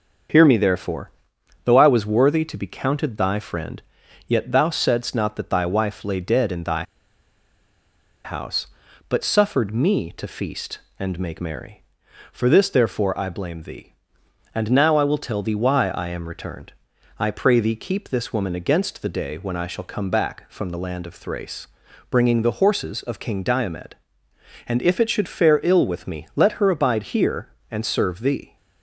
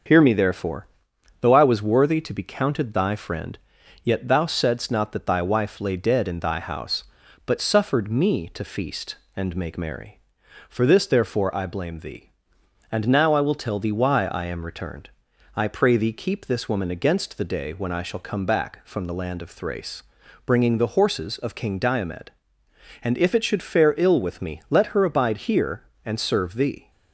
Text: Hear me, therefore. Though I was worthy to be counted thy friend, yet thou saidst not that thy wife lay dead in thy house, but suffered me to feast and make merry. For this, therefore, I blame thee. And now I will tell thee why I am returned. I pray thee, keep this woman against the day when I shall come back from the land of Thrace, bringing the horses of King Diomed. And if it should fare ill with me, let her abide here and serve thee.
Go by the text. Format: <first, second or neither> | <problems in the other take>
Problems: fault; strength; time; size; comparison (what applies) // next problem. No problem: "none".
second | starts louder than the rest; until 1.8 s; 6.5 dB; also in the second // pauses between "thy" and "house"; strong; at 6.8 s; 1.4 s long